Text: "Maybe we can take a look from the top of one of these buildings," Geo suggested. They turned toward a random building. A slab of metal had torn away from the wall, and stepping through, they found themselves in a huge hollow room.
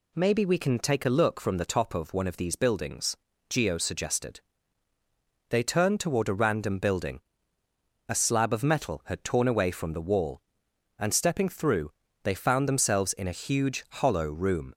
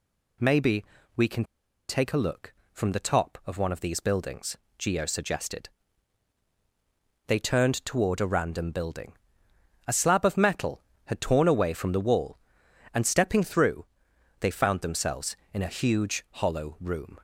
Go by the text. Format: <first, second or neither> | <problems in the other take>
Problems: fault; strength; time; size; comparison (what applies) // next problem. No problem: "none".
first | pauses between "Maybe" and "we"; slight; at 0.8 s; 0.32 s long // pauses between "can" and "take"; at 1.4 s; 0.44 s long